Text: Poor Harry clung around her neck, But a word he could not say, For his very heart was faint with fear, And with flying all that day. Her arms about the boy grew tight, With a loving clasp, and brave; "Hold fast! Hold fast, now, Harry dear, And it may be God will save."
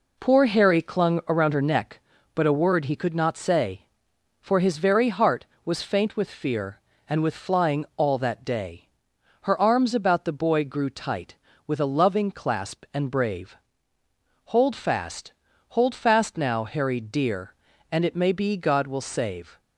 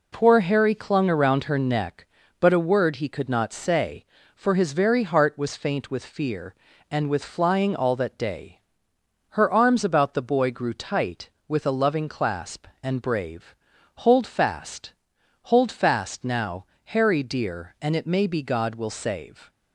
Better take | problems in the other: neither | none

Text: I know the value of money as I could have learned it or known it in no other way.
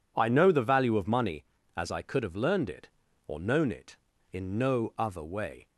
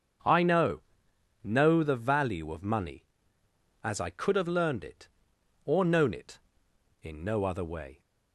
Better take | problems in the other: first | starts louder than the rest; strong; until 1.8 s; 7.5 dB // says "know" twice; at 1.4 s

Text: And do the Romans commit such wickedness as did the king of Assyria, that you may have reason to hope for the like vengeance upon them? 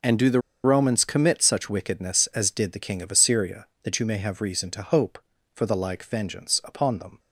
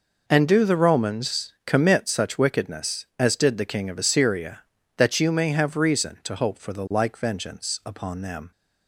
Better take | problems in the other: second | pauses between "the" and "Romans"; slight; at 0.4 s; 0.23 s long

